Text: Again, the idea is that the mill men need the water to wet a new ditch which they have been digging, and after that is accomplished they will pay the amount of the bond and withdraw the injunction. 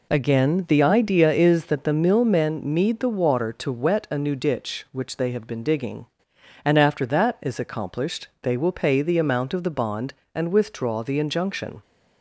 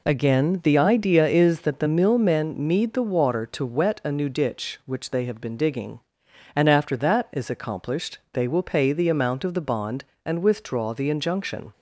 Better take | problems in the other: neither | none

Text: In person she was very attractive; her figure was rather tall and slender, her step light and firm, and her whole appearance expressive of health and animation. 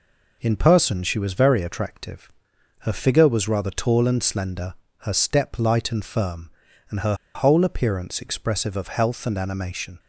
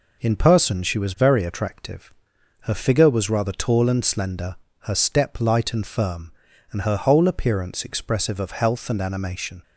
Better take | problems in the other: second | pauses between "her" and "whole"; slight; at 7.1 s; 0.20 s long

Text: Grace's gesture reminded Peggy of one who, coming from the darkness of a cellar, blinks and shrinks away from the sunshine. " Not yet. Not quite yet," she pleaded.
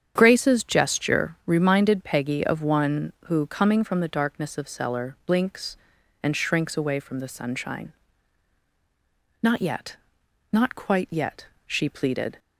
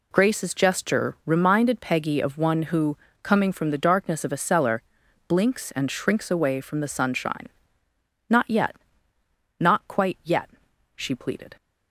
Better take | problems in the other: second | starts louder than the rest; strong; until 1.1 s; 9 dB // skips "a"; at 4.6 s

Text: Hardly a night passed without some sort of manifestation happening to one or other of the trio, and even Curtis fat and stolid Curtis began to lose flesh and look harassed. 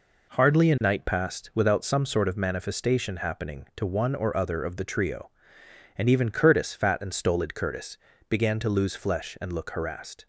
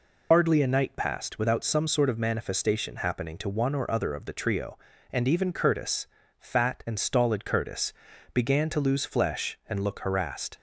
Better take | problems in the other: first | loses the start of "Hardly"; at 0.3 s; 80 ms // pauses between "Curtis" and "fat"; slight; at 6.0 s; 0.32 s long // pauses between "Curtis" and "began"; at 7.9 s; 0.40 s long; slight in the first

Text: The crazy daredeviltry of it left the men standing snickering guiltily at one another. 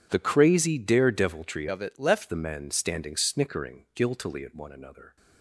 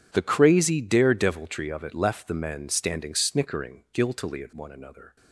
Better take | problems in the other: second | changes voice from "of" to "left"; from 1.6 to 2.2 s; 0.6 s long

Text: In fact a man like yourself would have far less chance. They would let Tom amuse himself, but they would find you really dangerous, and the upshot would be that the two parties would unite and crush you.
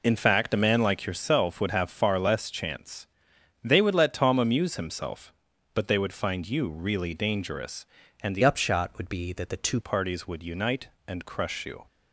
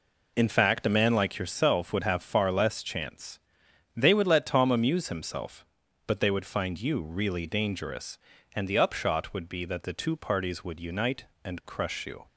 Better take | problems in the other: second | changes voice from "upshot" to "two"; from 8.4 to 9.7 s; 1.3 s long

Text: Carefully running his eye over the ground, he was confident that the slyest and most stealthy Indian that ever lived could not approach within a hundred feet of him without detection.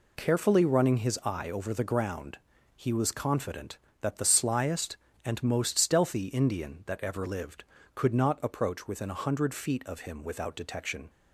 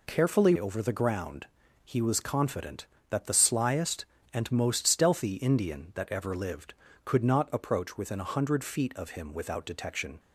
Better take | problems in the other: first | skips "running his eye"; at 0.5 s

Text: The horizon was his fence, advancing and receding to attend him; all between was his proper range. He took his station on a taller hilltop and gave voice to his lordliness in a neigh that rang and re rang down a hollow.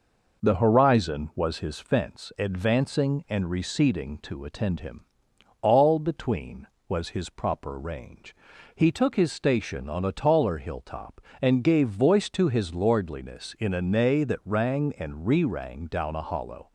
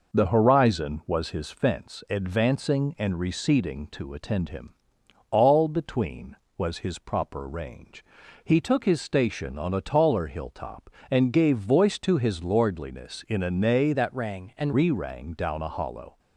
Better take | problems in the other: first | changes voice from "that" to "and"; from 13.9 to 14.7 s; 0.8 s long

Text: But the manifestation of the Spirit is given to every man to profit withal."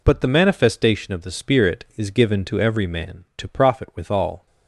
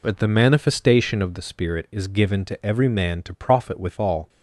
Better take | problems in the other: neither | none

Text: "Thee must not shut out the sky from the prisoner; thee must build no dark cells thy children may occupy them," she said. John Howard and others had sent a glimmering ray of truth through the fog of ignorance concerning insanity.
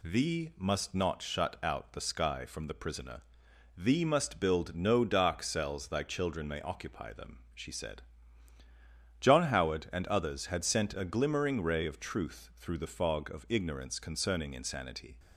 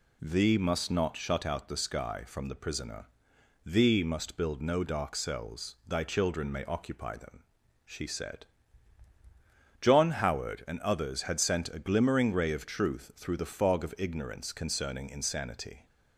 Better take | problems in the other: neither | none

